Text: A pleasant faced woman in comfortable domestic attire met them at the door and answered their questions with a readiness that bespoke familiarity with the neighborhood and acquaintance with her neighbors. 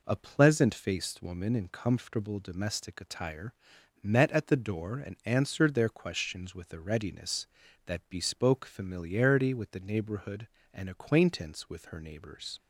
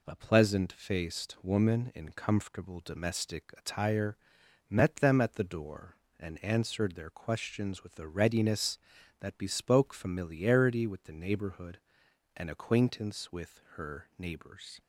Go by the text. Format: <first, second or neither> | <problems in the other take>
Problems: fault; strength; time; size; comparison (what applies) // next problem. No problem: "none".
second | pauses between "attire" and "met"; noticeable; at 3.5 s; 0.50 s long; noticeable in the second // skips "them"; at 4.3 s